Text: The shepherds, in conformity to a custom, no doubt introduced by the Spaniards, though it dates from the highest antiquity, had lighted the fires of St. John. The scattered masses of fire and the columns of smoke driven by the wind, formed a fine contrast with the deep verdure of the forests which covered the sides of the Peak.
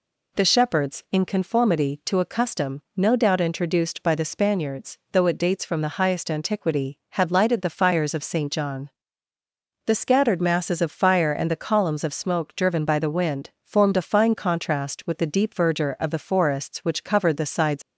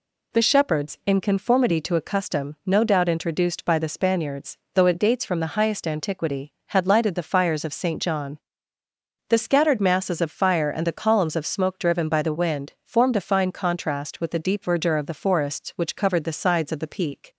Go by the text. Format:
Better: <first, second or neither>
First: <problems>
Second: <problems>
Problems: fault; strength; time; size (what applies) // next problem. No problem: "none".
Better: second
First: stops before "of the Peak"; at 17.8 s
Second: none